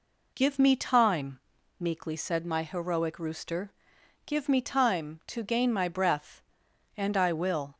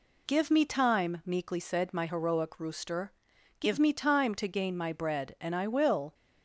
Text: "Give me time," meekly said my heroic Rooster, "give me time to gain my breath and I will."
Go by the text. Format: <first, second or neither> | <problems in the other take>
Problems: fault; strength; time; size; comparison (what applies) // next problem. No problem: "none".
first | says "bread" for "breath"; at 4.9 s